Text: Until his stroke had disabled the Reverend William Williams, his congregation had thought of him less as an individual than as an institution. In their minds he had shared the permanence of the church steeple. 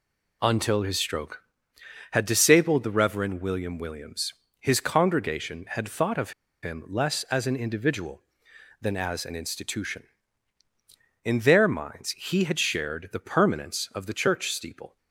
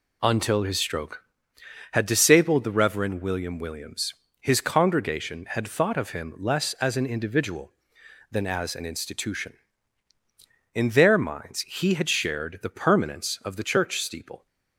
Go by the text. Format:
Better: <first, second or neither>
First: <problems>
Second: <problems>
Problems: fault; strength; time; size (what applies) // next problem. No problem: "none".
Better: second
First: pauses between "of" and "him"; slight; at 6.3 s; 0.31 s long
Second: none